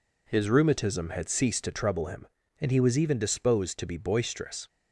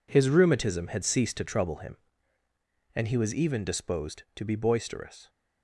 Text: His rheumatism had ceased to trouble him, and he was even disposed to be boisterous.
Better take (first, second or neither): first